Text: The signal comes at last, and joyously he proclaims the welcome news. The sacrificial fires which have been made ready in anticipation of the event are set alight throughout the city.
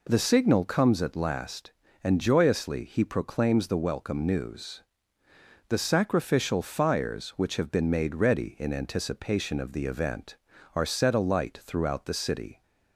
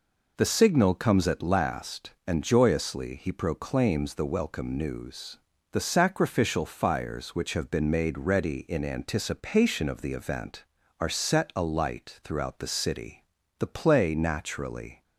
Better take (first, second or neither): first